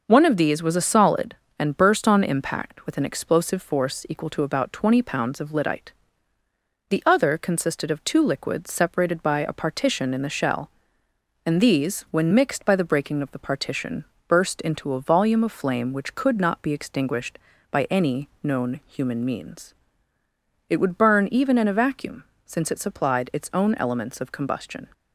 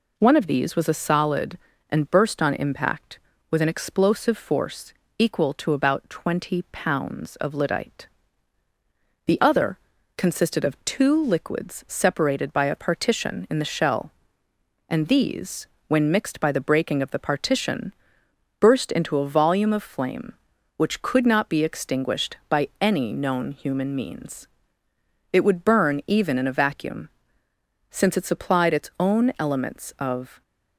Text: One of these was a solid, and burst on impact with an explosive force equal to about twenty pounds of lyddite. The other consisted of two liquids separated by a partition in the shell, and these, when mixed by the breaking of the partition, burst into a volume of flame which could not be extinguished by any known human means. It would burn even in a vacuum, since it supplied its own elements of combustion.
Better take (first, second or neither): first